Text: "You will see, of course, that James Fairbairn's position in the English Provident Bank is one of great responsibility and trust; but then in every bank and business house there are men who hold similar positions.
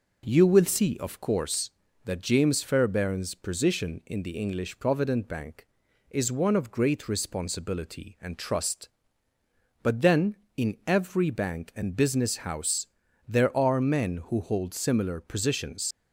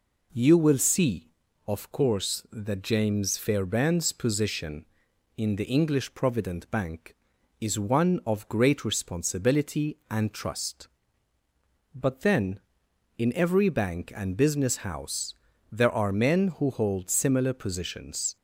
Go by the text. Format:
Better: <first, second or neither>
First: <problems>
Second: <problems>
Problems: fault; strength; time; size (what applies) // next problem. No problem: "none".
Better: second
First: pauses between "house" and "there"; at 12.8 s; 0.42 s long // leaves "positions" unfinished; at 15.9 s; 75 ms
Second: pauses between "house" and "there"; at 15.3 s; 0.38 s long